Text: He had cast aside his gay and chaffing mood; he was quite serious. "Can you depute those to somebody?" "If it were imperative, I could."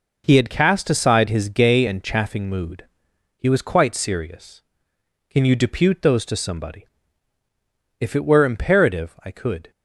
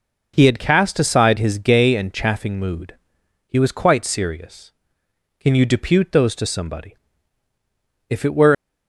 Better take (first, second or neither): first